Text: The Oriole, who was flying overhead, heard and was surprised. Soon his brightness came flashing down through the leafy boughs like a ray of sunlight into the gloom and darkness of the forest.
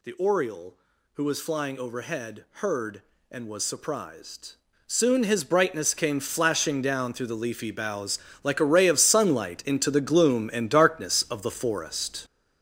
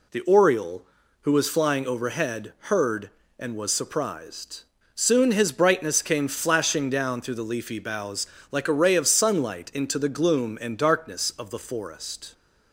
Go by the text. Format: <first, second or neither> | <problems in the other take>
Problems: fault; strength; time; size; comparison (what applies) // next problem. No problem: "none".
second | gets louder; strong; throughout; 8.5 dB // pauses between "boughs" and "like"; slight; at 8.1 s; 0.24 s long; slight in the second